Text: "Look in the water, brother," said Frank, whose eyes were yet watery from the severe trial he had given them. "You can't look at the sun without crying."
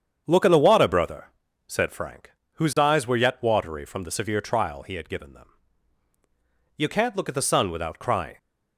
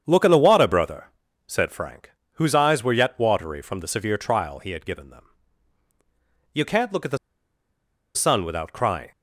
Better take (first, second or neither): first